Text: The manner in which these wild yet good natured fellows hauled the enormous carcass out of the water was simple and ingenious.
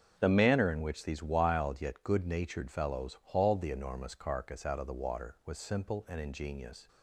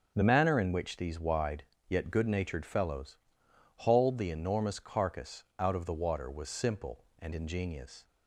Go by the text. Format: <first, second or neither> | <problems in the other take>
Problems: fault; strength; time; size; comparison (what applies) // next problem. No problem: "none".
first | starts louder than the rest; until 1.1 s; 6.5 dB; also in the first // says "wide" for "wild"; at 1.1 s // pauses between "fellows" and "hauled"; noticeable; at 3.1 s; 0.60 s long